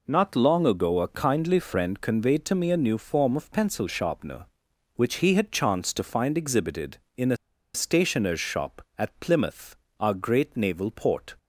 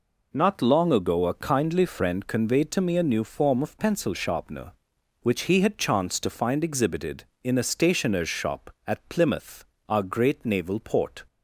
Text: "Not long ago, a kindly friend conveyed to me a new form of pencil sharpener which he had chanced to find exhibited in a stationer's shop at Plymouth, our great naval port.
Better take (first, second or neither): second